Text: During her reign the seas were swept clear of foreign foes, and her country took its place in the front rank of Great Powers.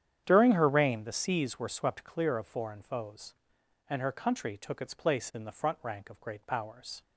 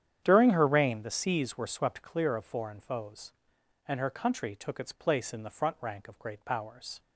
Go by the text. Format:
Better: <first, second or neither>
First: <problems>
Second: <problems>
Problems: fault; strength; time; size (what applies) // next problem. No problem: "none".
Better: neither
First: starts louder than the rest; strong; until 1.2 s; 9.5 dB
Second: starts louder than the rest; strong; until 1.2 s; 9.5 dB